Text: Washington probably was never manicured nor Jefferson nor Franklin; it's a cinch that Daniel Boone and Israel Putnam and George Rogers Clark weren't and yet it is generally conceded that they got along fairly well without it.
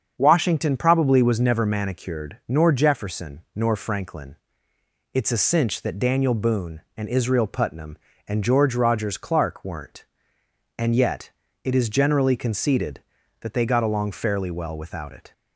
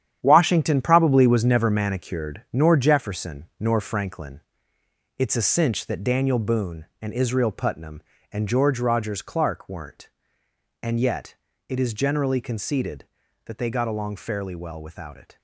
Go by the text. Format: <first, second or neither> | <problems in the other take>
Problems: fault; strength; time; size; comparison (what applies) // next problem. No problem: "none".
first | gets quieter; strong; throughout; 10 dB // starts louder than the rest; strong; until 1.2 s; 9.5 dB; also in the first // pauses between "yet" and "it"; slight; at 11.3 s; 0.34 s long; slight in the first